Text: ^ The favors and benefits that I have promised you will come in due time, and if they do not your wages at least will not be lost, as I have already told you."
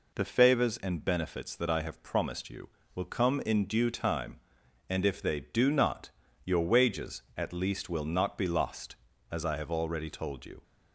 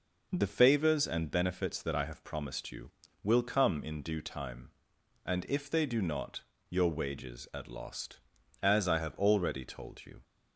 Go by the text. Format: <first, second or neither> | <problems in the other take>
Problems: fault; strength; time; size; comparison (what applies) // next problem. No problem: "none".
first | pauses between "not" and "your"; slight; at 6.4 s; 0.28 s long; slight in the first // skips "least will not be"; at 7.6 s